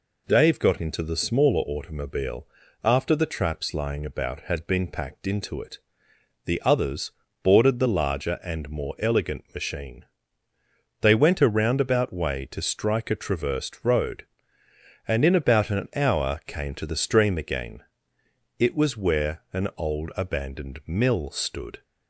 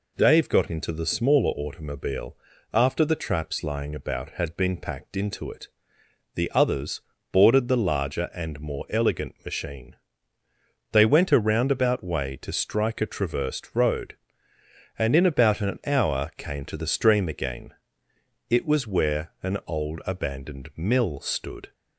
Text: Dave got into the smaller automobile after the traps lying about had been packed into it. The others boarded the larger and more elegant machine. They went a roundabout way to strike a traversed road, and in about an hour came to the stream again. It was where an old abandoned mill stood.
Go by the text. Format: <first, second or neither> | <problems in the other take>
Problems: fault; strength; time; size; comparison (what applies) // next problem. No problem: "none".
neither | pauses between "automobile" and "after"; slight; the same in both // pauses between "others" and "boarded"; slight; the same in both